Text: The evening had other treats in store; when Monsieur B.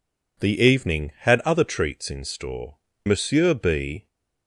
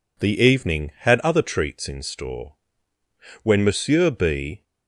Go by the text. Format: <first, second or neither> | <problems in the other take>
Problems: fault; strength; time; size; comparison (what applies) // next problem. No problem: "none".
second | skips "when"; at 2.9 s